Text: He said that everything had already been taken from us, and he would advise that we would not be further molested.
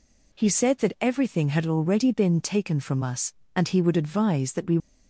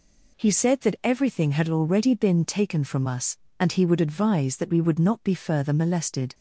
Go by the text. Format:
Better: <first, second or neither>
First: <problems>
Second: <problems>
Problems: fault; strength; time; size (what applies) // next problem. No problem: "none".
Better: second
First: stops before "would not be further molested"; at 4.7 s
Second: none